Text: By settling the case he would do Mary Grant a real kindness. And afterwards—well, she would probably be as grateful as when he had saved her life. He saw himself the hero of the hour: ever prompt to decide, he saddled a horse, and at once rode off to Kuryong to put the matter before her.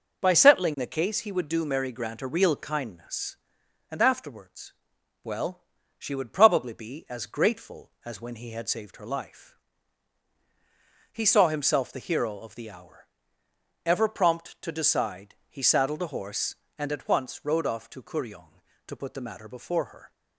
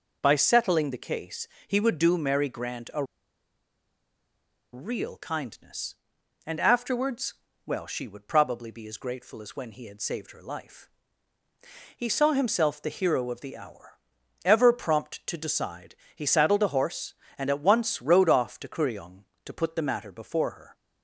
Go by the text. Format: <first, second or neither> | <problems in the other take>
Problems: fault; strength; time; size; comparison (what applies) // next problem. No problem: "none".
first | pauses between "case" and "he"; slight; at 1.4 s; 0.20 s long // pauses between "a" and "real"; strong; at 3.0 s; 1.6 s long